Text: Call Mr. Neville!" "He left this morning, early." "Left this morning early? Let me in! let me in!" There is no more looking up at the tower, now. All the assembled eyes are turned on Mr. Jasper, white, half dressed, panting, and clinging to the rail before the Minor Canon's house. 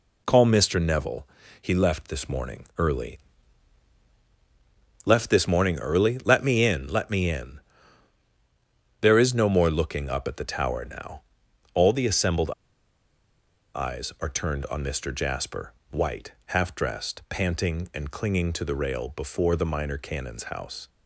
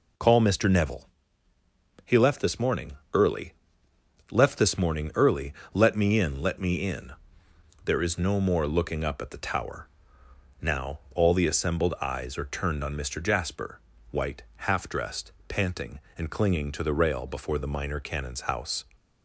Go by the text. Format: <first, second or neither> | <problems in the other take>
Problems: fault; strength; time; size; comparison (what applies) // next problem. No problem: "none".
second | pauses between "assembled" and "eyes"; at 12.4 s; 1.2 s long